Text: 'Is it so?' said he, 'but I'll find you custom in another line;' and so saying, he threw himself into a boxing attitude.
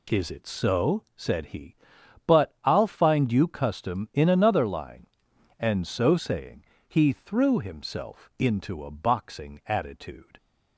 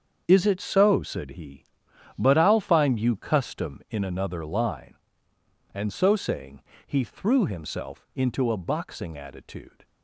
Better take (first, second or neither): first